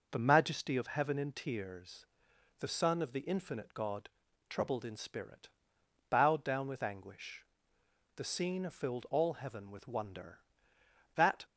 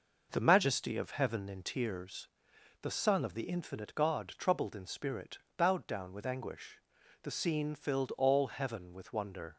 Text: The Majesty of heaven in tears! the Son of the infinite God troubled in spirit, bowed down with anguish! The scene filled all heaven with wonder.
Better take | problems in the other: second | pauses between "God" and "troubled"; at 4.0 s; 0.40 s long // goes on to say "That"; slight; from 11.1 s on; 0.24 s long

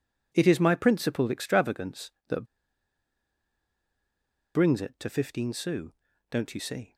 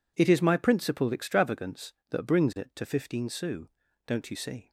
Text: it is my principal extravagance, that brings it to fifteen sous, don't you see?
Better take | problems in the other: second | pauses between "that" and "brings"; strong; at 2.4 s; 2.1 s long

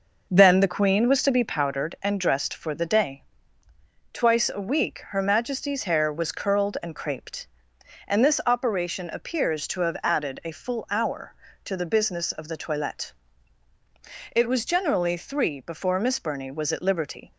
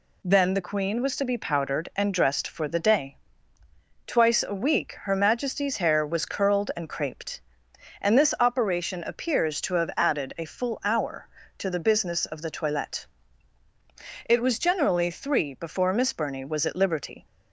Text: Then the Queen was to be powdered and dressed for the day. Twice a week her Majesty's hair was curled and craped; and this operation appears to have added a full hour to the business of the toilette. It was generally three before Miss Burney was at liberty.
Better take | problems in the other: second | starts louder than the rest; noticeable; until 1.6 s; 5.5 dB

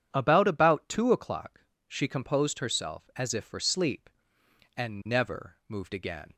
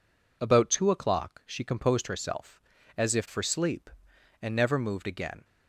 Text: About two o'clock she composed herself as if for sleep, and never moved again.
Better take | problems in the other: second | starts louder than the rest; strong; until 1.1 s; 9 dB // says "About" twice; at 0.4 s // pauses between "o'clock" and "she"; slight; at 1.6 s; 0.26 s long

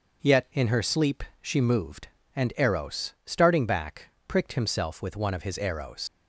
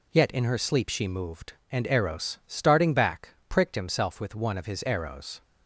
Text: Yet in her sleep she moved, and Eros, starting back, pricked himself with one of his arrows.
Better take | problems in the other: second | starts louder than the rest; noticeable; until 1.4 s; 6 dB // pauses between "sleep" and "she"; slight; at 1.2 s; 0.16 s long // leaves "arrows" unfinished; at 6.0 s; 125 ms

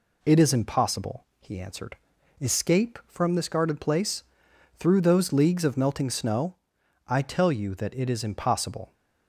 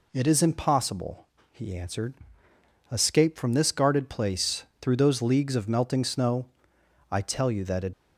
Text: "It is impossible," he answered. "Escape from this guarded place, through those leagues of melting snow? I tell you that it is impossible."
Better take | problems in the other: first | stops before "is impossible"; at 7.9 s

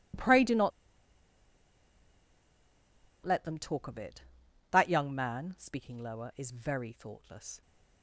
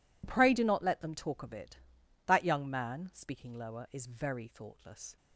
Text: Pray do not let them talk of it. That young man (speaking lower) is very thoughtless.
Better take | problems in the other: second | pauses between "not" and "let"; strong; at 0.7 s; 2.5 s long

